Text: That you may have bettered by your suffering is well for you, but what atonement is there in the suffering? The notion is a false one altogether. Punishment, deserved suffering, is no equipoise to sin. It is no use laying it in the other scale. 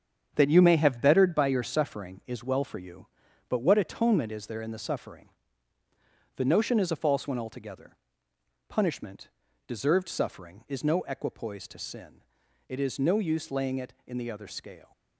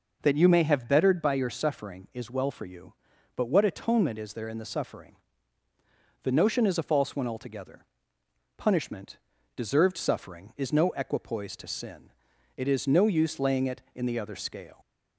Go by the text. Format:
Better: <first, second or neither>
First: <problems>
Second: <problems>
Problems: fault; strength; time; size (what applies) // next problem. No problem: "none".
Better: second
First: gets quieter; strong; throughout; 7.5 dB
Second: none